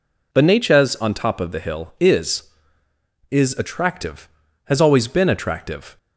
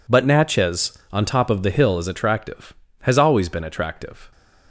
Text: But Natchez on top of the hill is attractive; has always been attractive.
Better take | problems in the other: second | says "is" twice; at 3.2 s

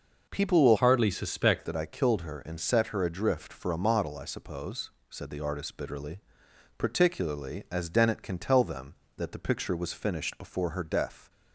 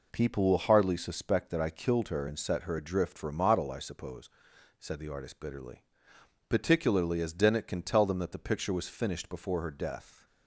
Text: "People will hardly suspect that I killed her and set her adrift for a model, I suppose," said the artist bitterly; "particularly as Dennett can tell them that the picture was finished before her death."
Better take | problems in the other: second | changes voice from "hardly" to "suspect"; from 0.7 to 1.6 s; 0.9 s long

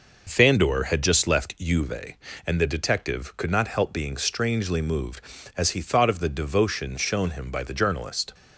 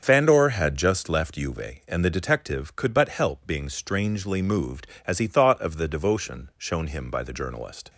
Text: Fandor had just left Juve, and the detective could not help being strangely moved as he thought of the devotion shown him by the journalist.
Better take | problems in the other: first | starts louder than the rest; until 1.0 s; 7 dB // says "but" for "not"; at 2.9 s

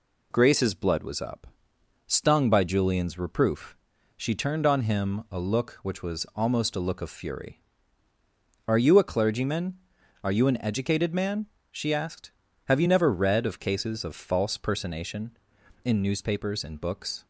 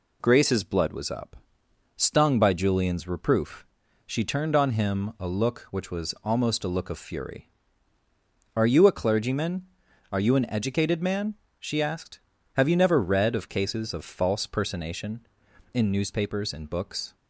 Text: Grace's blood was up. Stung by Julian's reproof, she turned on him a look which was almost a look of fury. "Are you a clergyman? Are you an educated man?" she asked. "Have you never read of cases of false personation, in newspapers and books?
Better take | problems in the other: neither | none

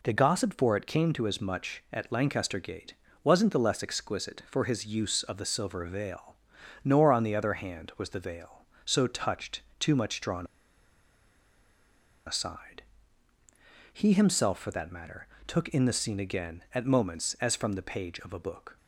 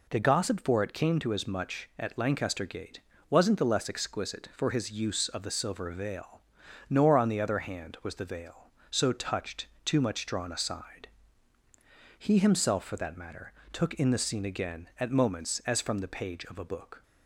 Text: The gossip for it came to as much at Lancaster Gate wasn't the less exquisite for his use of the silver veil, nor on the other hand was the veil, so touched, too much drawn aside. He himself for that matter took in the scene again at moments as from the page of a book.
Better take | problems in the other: second | pauses between "Gate" and "wasn't"; slight; at 2.9 s; 0.28 s long; slight in the second // pauses between "drawn" and "aside"; strong; at 10.4 s; 1.8 s long // pauses between "matter" and "took"; slight; at 15.2 s; 0.20 s long; slight in the second

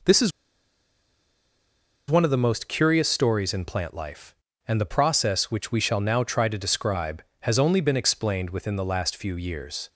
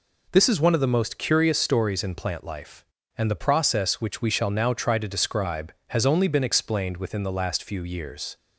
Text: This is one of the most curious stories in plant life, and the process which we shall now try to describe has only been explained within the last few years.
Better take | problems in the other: second | pauses between "is" and "one"; strong; at 0.3 s; 1.7 s long

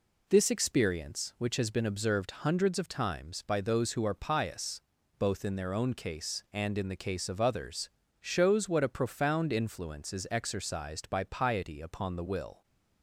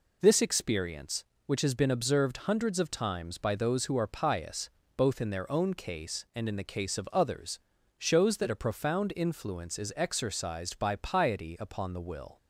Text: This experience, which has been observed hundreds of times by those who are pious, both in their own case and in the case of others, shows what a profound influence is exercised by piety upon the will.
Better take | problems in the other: first | says "that" for "what"; at 8.3 s

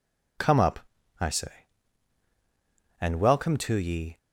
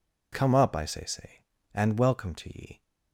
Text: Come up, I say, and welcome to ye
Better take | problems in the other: first | says "say" twice; at 1.0 s

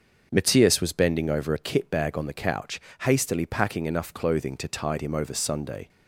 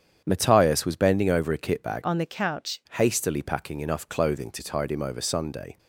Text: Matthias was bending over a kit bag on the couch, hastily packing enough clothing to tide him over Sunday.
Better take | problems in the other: first | starts louder than the rest; strong; until 1.2 s; 8.5 dB; also in the first // changes voice from "on" to "couch"; from 2.0 to 2.8 s; 0.8 s long

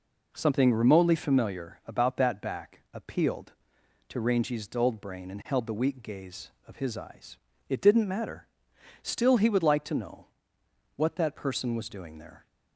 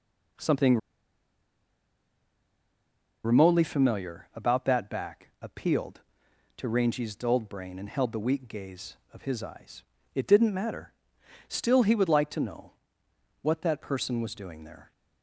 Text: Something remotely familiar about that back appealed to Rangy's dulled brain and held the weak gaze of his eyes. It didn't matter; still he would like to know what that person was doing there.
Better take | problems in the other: first | pauses between "Something" and "remotely"; strong; at 0.7 s; 2.4 s long // pauses between "know" and "what"; noticeable; at 12.7 s; 0.70 s long; noticeable in the first

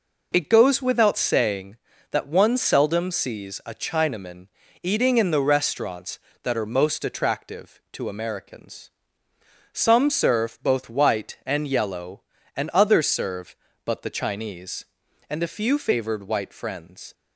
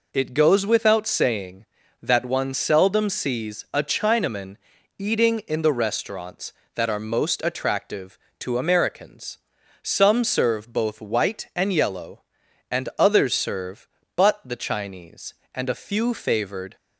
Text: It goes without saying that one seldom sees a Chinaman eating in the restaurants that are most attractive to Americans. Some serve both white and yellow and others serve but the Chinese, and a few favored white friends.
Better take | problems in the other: first | pauses between "Chinaman" and "eating"; at 4.5 s; 0.42 s long; slight in the first // stops before "white friends"; at 16.7 s

